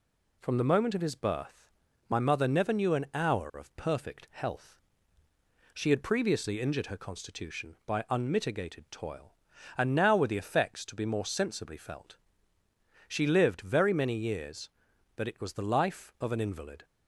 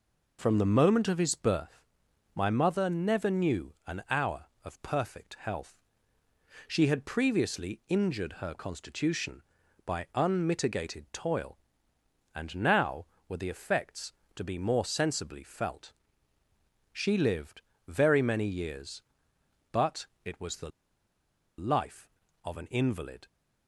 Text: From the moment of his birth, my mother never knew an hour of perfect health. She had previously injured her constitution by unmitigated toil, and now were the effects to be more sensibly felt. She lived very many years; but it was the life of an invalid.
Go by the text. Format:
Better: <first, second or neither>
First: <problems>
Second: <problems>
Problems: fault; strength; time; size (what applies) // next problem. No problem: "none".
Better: first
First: none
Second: pauses between "lived" and "very"; slight; at 17.5 s; 0.26 s long // pauses between "but" and "it"; slight; at 20.0 s; 0.18 s long // pauses between "the" and "life"; noticeable; at 20.6 s; 0.88 s long